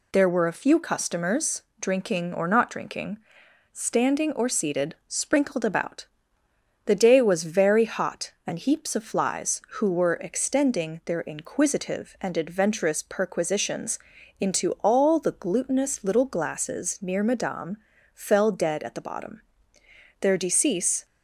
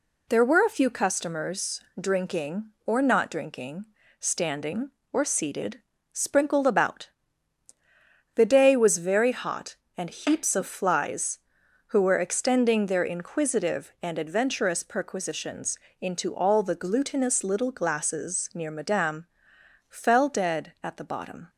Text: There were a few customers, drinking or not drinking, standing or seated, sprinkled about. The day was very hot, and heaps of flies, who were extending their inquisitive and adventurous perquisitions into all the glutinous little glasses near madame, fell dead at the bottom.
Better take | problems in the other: second | pauses between "perquisitions" and "into"; at 13.9 s; 0.40 s long; slight in the second // goes on to say "Their decease"; noticeable; from 20.2 s on; 0.84 s long

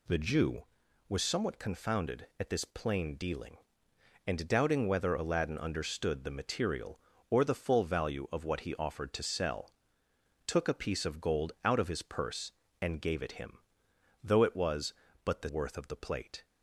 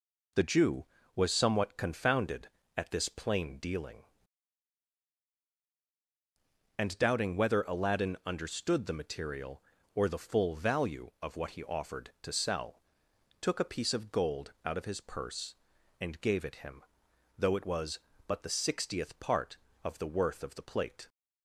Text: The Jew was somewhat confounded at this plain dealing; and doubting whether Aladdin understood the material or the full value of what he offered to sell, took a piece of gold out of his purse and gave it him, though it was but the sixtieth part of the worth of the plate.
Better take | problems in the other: second | skips "sixtieth part of the"; at 15.4 s

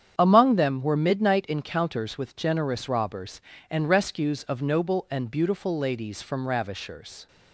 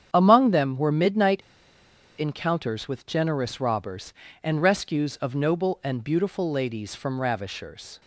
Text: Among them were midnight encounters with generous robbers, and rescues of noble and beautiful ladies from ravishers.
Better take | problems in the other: first | starts louder than the rest; strong; until 1.1 s; 8.5 dB; strong in the first // pauses between "midnight" and "encounters"; noticeable; at 1.4 s; 0.76 s long

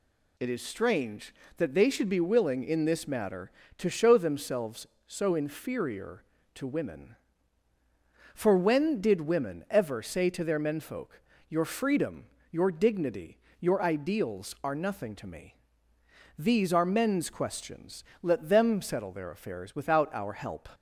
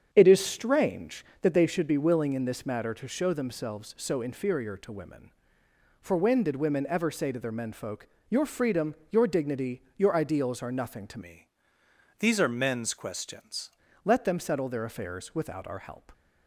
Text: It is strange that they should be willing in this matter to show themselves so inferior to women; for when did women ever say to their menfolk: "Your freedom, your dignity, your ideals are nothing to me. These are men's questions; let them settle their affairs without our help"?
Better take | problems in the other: first | starts louder than the rest; strong; until 1.1 s; 8 dB // changes voice from "me" to "questions"; from 11.2 to 13.6 s; 2.4 s long

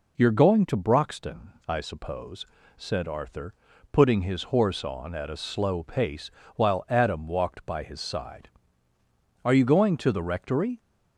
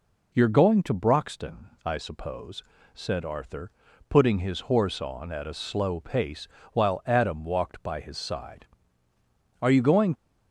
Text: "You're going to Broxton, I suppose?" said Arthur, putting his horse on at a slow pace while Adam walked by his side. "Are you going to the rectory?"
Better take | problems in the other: first | pauses between "pace" and "while"; slight; at 6.4 s; 0.24 s long; slight in the first // stops before "to the rectory"; at 10.1 s

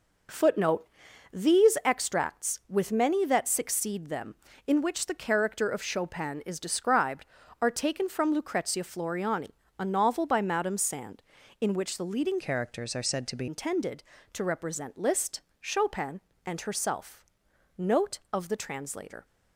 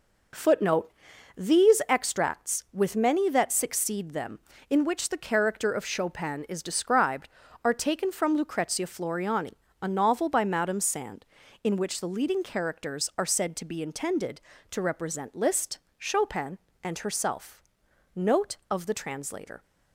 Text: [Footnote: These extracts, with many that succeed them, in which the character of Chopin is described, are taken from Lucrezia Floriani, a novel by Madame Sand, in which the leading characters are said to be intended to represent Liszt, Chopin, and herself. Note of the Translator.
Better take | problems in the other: second | changes voice from "characters" to "be"; from 12.3 to 13.4 s; 1.1 s long

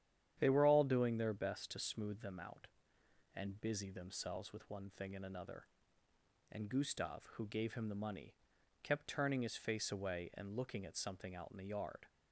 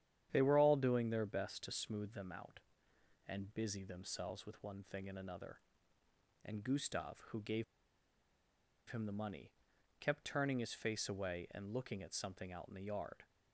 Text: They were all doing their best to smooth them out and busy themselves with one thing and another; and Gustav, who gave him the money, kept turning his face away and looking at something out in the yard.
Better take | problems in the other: first | starts louder than the rest; strong; until 1.3 s; 10 dB; strong in the first // pauses between "gave" and "him"; strong; at 7.6 s; 1.2 s long

